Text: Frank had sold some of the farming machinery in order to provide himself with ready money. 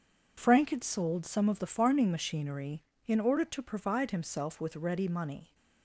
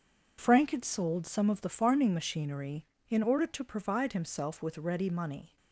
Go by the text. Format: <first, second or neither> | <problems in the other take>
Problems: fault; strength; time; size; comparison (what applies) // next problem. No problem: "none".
neither | none